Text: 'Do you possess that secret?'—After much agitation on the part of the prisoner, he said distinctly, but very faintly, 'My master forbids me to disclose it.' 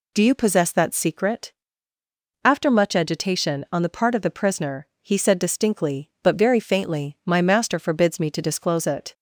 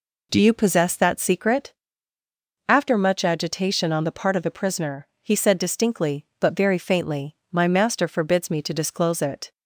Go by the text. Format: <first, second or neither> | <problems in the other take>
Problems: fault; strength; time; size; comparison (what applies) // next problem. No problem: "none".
neither | none